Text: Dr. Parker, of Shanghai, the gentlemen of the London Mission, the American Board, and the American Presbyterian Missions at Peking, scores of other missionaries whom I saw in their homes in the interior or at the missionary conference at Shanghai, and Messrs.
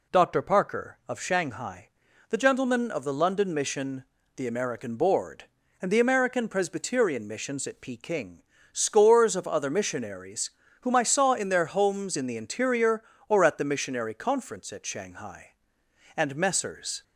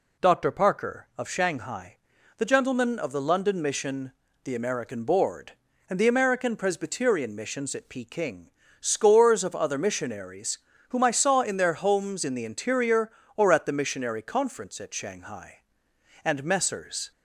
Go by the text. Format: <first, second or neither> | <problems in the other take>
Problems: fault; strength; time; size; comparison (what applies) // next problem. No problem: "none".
neither | pauses between "missionaries" and "whom"; slight; the same in both